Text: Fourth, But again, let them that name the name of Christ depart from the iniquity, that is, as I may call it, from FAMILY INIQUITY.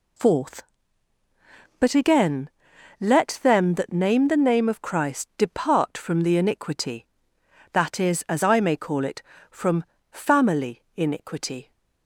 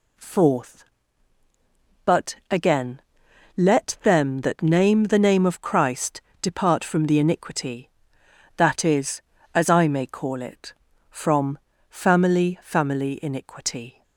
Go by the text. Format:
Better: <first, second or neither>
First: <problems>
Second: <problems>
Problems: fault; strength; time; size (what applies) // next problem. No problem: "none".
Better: first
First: pauses between "from" and "FAMILY"; slight; at 9.8 s; 0.30 s long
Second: pauses between "Christ" and "depart"; slight; at 6.2 s; 0.20 s long // pauses between "from" and "FAMILY"; slight; at 11.5 s; 0.32 s long // says "FAMILY" twice; at 12.6 s